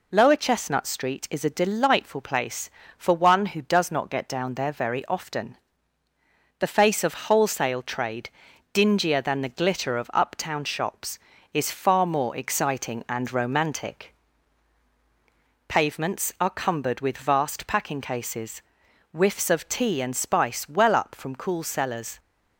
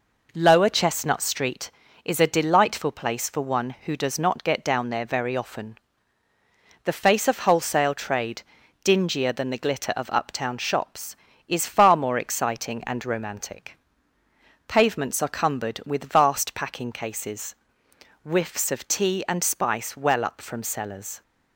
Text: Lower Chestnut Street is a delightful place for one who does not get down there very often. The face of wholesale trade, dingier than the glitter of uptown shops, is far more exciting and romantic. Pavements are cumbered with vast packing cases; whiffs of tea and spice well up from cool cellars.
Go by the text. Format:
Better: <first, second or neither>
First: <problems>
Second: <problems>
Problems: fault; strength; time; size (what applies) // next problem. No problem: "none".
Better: first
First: none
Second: skips "cool"; at 20.6 s